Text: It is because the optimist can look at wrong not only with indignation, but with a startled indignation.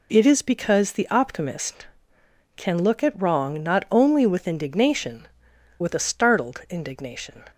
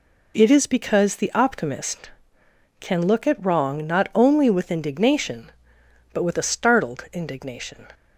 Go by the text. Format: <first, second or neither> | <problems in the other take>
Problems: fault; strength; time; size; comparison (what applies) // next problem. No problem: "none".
second | skips "but"; at 5.5 s